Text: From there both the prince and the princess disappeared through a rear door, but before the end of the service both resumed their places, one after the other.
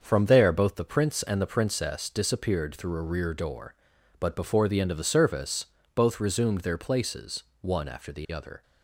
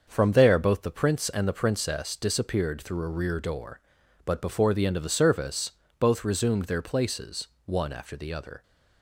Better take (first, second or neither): neither